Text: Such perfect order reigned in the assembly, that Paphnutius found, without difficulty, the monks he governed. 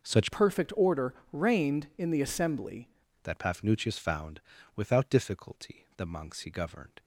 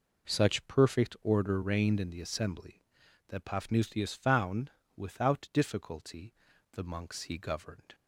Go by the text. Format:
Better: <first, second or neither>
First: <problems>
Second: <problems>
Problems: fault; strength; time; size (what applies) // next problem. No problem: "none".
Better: second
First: changes voice from "perfect" to "assembly"; from 0.3 to 2.8 s; 2.5 s long // pauses between "order" and "reigned"; slight; at 1.1 s; 0.18 s long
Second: none